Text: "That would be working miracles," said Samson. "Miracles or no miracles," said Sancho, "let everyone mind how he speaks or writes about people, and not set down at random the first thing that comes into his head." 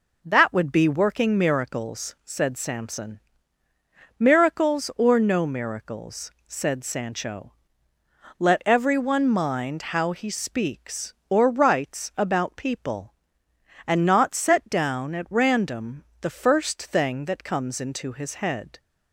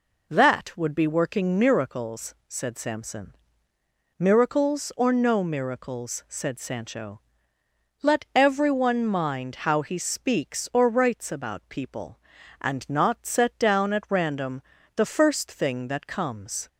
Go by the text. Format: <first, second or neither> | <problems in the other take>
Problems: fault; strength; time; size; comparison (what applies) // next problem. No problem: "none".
first | pauses between "random" and "the"; slight; at 14.6 s; 0.34 s long; slight in the first // stops before "into his head"; at 16.6 s